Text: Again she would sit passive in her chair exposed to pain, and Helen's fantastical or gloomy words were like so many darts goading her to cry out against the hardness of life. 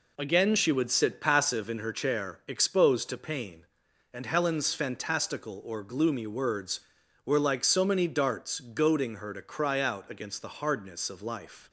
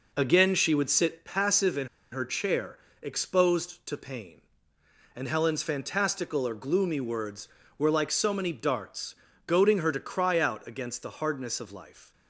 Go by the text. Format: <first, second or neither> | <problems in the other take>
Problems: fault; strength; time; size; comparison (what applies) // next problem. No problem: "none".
first | pauses between "in" and "her"; slight; at 1.8 s; 0.25 s long // pauses between "chair" and "exposed"; slight; at 2.7 s; 0.26 s long // pauses between "darts" and "goading"; slight; at 9.1 s; 0.32 s long